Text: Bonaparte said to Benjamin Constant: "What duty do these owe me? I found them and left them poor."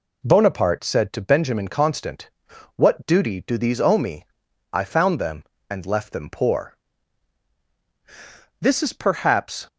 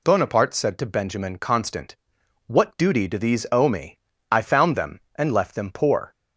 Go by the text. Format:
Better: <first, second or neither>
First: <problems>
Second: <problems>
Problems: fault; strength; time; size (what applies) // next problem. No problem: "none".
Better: second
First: goes on to say "This is perhaps"; noticeable; from 8.5 s on; 1.0 s long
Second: none